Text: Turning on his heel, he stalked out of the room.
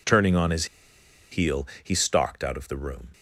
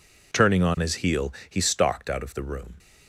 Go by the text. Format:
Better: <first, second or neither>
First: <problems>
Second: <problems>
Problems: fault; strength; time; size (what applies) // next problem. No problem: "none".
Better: second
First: pauses between "his" and "heel"; noticeable; at 0.6 s; 0.65 s long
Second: none